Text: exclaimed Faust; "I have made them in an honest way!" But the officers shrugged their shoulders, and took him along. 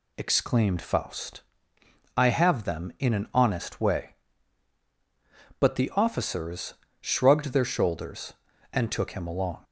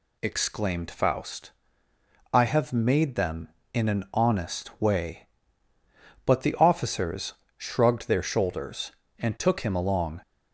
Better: second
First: skips "made"; at 2.6 s // pauses between "officers" and "shrugged"; slight; at 6.7 s; 0.26 s long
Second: pauses between "officers" and "shrugged"; slight; at 7.3 s; 0.22 s long

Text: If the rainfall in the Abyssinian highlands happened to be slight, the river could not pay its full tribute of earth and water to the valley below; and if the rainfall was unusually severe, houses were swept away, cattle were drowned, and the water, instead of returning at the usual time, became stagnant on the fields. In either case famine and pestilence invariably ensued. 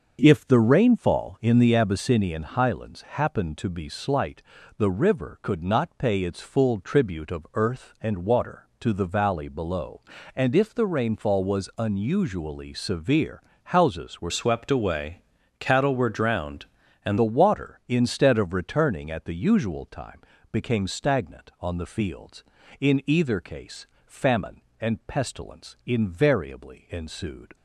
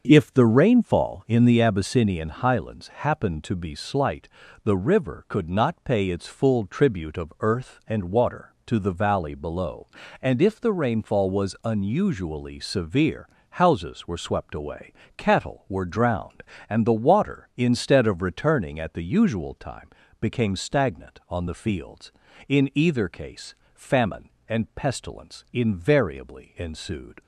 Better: second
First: starts louder than the rest; until 1.2 s; 6.5 dB // changes voice from "swept" to "and"; from 14.2 to 17.1 s; 2.9 s long // pauses between "case" and "famine"; slight; at 23.8 s; 0.18 s long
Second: starts louder than the rest; until 1.0 s; 6.5 dB // pauses between "case" and "famine"; slight; at 23.5 s; 0.18 s long

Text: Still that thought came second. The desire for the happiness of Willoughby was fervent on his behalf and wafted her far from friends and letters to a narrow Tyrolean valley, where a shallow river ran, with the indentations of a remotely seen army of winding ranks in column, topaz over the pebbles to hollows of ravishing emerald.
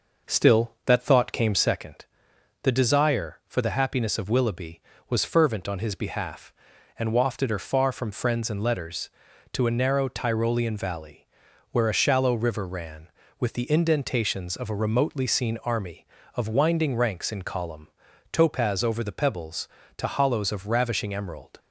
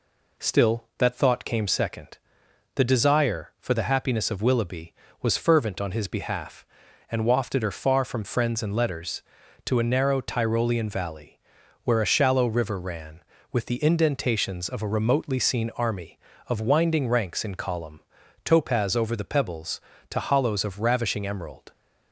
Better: second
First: starts louder than the rest; noticeable; until 1.8 s; 5.5 dB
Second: none

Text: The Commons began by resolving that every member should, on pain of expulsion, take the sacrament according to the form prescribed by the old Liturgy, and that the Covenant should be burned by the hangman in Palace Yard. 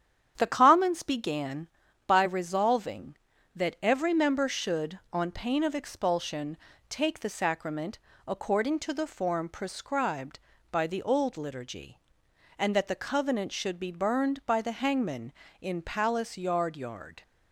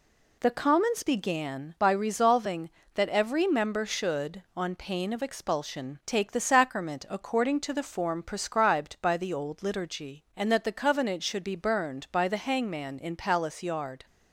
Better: second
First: starts louder than the rest; strong; until 1.3 s; 9 dB // pauses between "sacrament" and "according"; slight; at 7.9 s; 0.28 s long // says "Yard" twice; at 16.7 s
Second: none

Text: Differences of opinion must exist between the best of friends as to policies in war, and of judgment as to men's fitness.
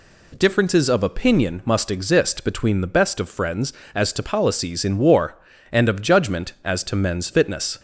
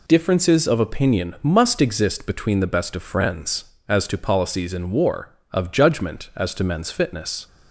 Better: first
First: none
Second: skips "and"; at 5.4 s

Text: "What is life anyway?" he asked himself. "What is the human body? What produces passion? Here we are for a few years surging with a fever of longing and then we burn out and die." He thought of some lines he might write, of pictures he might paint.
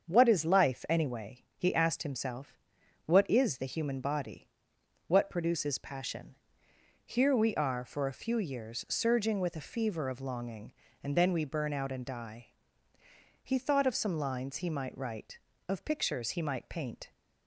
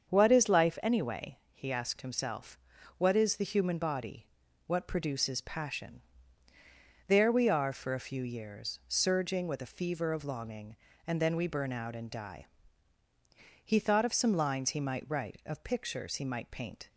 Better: first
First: starts louder than the rest; until 1.1 s; 7 dB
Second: starts louder than the rest; until 1.1 s; 7 dB // says "There" for "Here"; at 7.0 s

